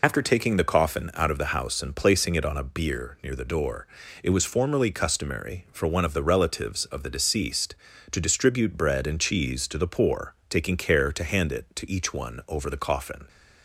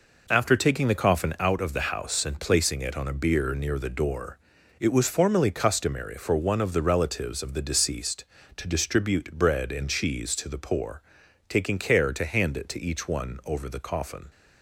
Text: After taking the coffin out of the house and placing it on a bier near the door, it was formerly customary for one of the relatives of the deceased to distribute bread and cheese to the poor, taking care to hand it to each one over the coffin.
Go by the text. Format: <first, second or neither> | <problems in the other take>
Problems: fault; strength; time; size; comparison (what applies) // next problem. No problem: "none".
second | loses the start of "After"; at 0.0 s; 55 ms